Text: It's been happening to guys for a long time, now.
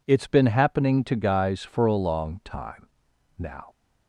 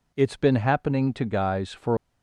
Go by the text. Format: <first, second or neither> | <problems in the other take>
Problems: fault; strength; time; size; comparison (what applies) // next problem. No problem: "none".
first | stops before "a long time now"; at 1.9 s